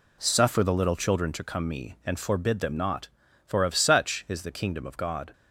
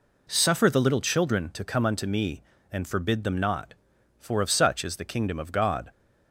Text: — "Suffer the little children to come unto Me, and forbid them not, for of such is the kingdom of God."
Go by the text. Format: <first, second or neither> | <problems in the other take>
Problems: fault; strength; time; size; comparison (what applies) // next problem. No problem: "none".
second | skips "unto"; at 1.6 s